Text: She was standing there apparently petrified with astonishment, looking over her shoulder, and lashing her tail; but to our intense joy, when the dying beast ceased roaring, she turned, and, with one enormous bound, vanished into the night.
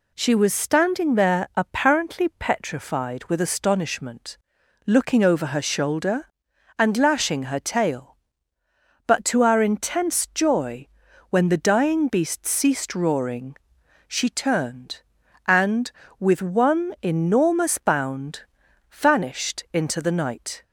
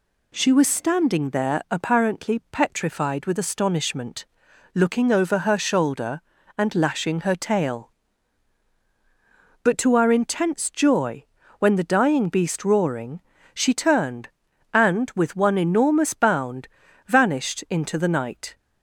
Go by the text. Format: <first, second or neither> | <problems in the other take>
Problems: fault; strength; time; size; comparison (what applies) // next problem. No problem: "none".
first | skips "ceased"; at 12.6 s